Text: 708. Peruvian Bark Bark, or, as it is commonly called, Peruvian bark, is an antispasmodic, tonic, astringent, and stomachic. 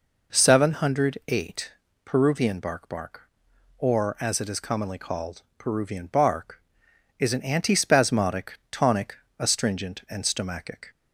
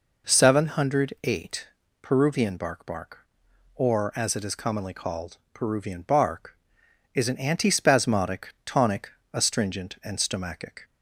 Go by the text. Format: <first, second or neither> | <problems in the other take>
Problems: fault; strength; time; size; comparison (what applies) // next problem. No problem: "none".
neither | none